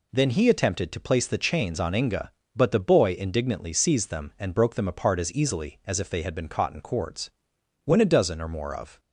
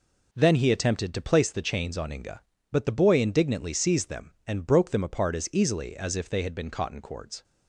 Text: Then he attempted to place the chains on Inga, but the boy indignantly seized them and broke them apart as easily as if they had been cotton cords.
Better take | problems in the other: second | goes on to say "When a dozen or more of"; noticeable; from 7.8 s on; 1.1 s long

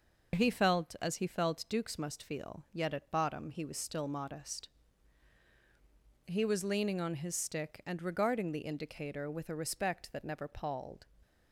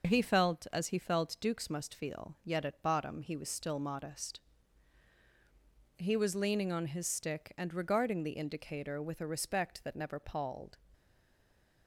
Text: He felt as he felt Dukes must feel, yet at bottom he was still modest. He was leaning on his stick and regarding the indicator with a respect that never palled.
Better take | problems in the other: first | stays silent after the last word; slight; from 10.9 s on; 0.9 s long

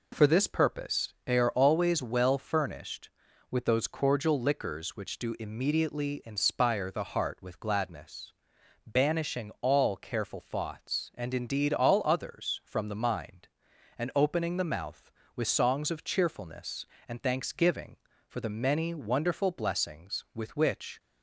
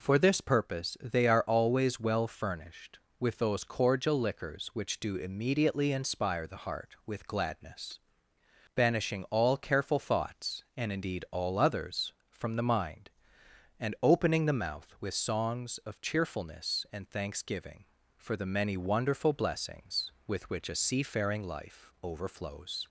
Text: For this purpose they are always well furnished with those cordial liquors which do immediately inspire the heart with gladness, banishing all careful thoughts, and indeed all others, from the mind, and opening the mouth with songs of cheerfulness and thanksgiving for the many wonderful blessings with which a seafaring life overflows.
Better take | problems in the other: second | stops before "a seafaring life overflows"; at 20.9 s

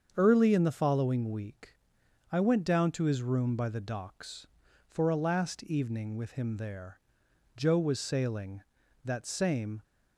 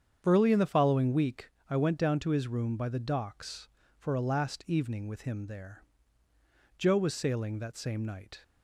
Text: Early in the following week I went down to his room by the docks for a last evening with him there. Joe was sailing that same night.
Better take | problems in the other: second | starts louder than the rest; until 1.1 s; 7 dB; strong in the second // pauses between "week" and "I"; noticeable; at 1.7 s; 0.58 s long; slight in the second // stops before "night"; at 9.8 s

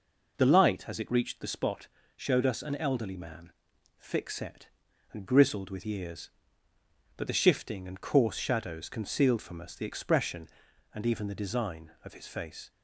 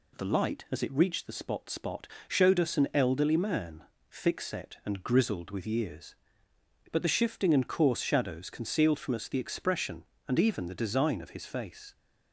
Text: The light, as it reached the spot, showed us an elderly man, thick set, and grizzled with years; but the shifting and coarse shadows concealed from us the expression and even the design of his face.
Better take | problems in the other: first | says "spot" twice; at 1.6 s

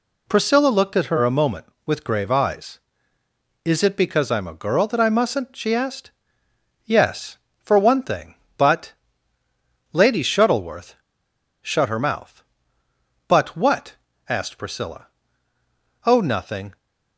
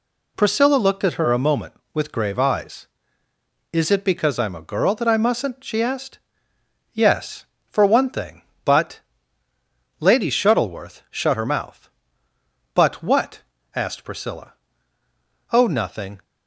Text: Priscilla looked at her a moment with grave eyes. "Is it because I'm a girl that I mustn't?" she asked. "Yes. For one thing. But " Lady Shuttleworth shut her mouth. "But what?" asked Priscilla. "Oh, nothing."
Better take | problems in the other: second | pauses between "Shuttleworth" and "shut"; noticeable; at 10.9 s; 0.66 s long

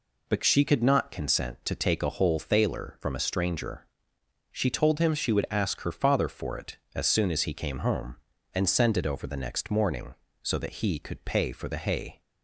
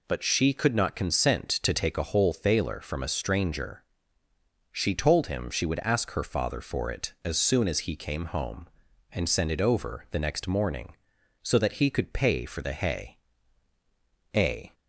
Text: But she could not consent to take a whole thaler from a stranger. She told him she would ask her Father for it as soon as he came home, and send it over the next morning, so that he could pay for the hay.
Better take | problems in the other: first | goes on to say "A"; slight; from 14.3 s on; 0.40 s long

